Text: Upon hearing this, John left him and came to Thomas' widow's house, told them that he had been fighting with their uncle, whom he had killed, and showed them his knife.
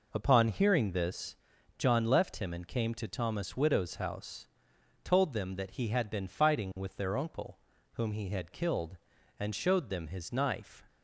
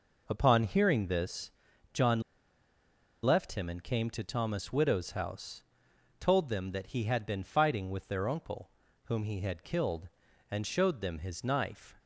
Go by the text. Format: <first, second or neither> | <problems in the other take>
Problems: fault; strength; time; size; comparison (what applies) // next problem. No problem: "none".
first | pauses between "John" and "left"; at 2.1 s; 1.0 s long